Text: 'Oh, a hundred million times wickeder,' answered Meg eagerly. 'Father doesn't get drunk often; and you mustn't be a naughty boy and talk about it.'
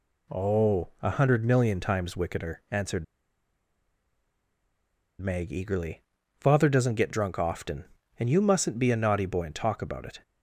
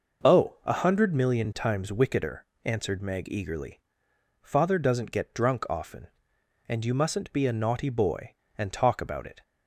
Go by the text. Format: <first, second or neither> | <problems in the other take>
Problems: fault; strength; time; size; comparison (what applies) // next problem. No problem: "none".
second | pauses between "answered" and "Meg"; strong; at 3.0 s; 2.1 s long